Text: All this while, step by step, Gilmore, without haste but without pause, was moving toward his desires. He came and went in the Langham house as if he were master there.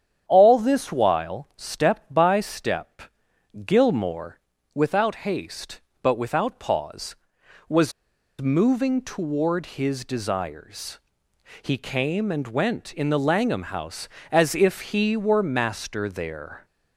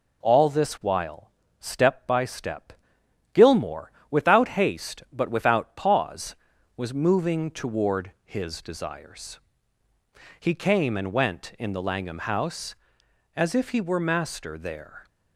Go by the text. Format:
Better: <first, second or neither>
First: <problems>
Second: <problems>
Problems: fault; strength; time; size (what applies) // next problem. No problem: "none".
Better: second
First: starts louder than the rest; strong; until 1.2 s; 9 dB // pauses between "was" and "moving"; noticeable; at 7.9 s; 0.49 s long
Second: none